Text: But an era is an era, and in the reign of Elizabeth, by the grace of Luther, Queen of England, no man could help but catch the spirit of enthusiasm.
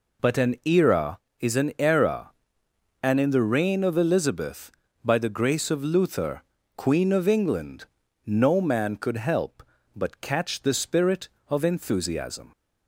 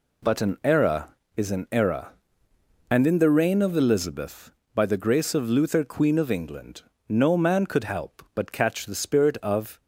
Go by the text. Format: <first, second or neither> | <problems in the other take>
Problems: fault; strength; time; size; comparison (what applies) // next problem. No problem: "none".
first | stops before "enthusiasm"; at 9.7 s